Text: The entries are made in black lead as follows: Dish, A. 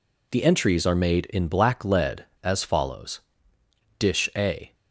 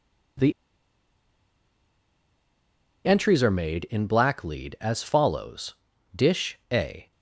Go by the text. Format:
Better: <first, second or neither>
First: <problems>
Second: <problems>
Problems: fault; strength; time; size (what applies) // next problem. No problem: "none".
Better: first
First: none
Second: pauses between "The" and "entries"; strong; at 0.5 s; 2.5 s long